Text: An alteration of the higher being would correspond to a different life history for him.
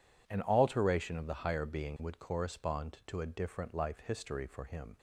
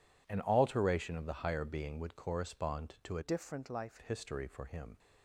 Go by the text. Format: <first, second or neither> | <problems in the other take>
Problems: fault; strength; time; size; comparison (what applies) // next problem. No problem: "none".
first | changes voice from "different" to "life"; from 3.2 to 3.9 s; 0.7 s long